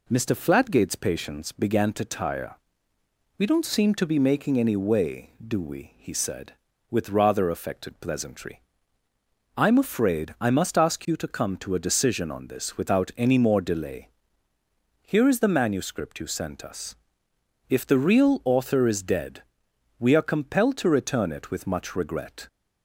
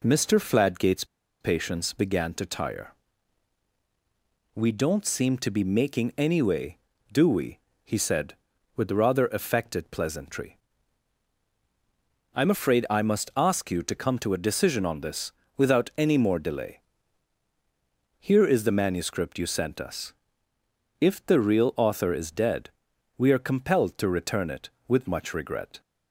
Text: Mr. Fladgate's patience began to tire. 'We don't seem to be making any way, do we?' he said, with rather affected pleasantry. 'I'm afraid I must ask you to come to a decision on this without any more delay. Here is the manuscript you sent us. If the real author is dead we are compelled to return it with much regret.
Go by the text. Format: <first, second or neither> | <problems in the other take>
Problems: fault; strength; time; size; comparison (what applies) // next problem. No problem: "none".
first | pauses between "Fladgate's" and "patience"; slight; at 1.0 s; 0.35 s long // pauses between "this" and "without"; slight; at 15.3 s; 0.24 s long // pauses between "dead" and "we"; noticeable; at 22.6 s; 0.48 s long; noticeable in the first